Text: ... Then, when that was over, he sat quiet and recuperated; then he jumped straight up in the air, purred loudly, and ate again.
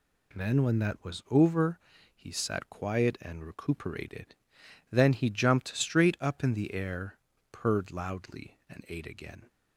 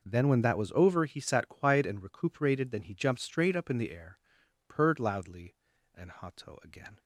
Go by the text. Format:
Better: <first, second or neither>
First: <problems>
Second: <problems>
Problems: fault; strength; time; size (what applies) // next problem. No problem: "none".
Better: first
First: none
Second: says "hato" for "ate"; at 6.1 s